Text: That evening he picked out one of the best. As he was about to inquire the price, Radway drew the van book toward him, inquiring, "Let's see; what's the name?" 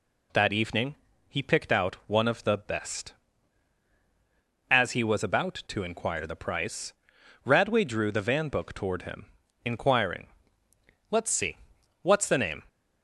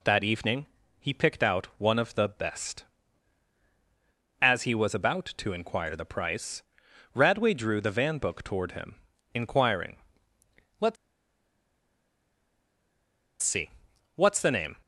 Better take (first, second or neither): first